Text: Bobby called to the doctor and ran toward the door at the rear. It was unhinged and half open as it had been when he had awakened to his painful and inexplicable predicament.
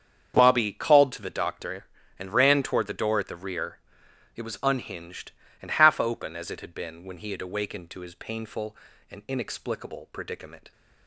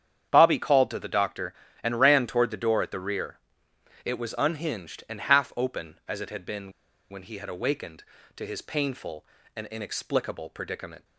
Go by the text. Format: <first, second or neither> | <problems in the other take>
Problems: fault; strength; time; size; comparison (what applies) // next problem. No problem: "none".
first | starts louder than the rest; strong; until 1.3 s; 8.5 dB; strong in the first // pauses between "been" and "when"; at 6.7 s; 0.38 s long